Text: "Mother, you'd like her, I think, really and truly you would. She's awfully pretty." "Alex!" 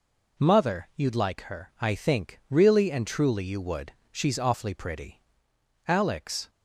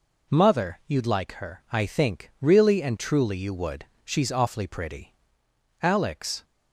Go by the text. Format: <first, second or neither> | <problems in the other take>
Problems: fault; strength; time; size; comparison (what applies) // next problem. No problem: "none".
neither | none